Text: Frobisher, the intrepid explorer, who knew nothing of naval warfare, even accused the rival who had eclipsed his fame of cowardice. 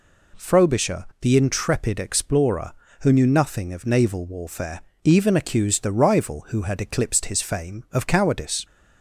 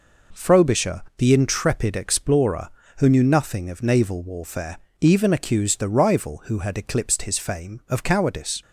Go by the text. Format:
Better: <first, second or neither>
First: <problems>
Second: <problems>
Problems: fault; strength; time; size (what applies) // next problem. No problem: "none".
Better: first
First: none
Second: gets quieter; noticeable; throughout; 5.5 dB